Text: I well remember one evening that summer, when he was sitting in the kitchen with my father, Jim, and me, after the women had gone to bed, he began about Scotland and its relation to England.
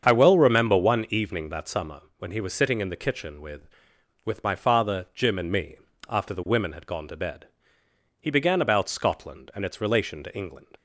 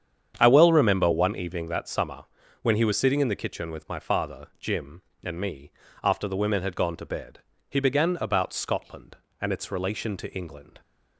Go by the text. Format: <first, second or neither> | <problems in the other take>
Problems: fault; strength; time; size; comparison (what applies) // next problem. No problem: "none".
second | starts louder than the rest; strong; until 1.0 s; 7 dB; strong in the second // says "with" twice; at 4.2 s